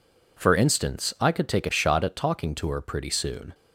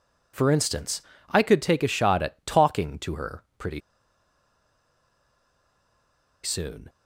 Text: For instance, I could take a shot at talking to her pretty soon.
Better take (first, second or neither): first